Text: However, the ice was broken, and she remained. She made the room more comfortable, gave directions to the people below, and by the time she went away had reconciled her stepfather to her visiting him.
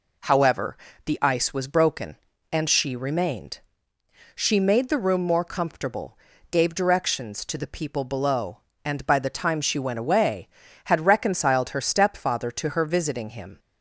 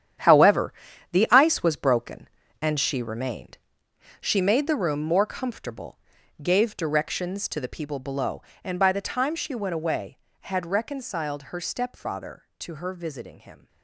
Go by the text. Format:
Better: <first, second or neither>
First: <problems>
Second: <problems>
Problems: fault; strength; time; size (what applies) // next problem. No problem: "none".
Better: first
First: none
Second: gets quieter; strong; throughout; 11 dB